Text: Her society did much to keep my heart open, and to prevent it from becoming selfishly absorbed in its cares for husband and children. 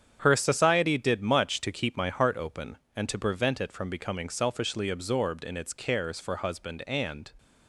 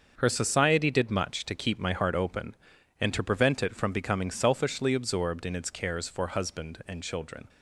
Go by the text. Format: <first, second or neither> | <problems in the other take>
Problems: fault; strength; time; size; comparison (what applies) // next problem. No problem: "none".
second | starts louder than the rest; strong; until 1.2 s; 8.5 dB; also in the second // stops before "children"; at 7.3 s